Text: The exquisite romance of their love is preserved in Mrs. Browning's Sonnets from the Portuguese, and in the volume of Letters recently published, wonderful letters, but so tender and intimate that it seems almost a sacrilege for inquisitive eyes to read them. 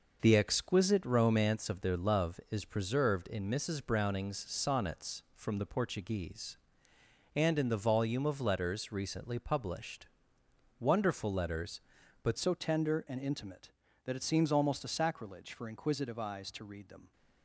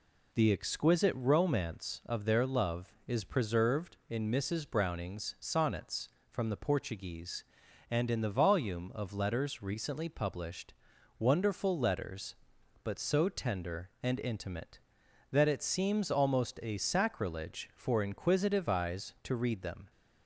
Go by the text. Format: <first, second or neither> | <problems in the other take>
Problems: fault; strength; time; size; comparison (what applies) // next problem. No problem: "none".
second | changes voice at "so"; from 12.3 s on; 4.8 s long